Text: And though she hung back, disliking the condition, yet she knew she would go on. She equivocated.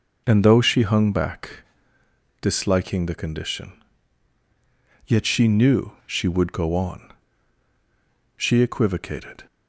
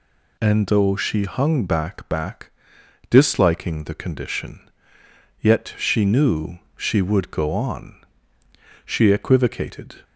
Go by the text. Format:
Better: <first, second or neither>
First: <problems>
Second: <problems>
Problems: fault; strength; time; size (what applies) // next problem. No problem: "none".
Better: first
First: none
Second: says "back" twice; at 2.0 s // pauses between "knew" and "she"; slight; at 6.5 s; 0.16 s long